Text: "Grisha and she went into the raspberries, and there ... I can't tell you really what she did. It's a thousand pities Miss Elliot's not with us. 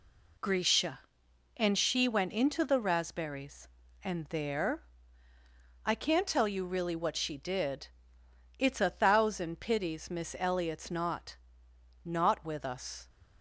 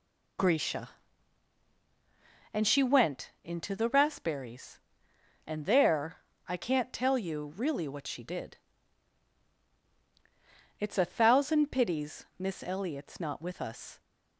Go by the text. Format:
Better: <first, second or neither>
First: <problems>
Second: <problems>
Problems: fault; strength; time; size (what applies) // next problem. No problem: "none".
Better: second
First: says "not" twice; at 12.0 s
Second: none